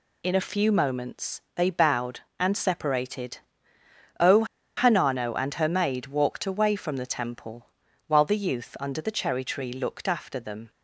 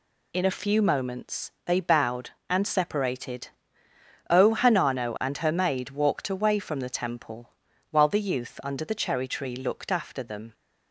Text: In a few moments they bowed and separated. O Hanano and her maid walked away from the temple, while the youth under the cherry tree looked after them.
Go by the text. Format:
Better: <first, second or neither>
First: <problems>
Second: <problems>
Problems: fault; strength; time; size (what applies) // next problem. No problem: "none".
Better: second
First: pauses between "O" and "Hanano"; slight; at 4.4 s; 0.33 s long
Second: none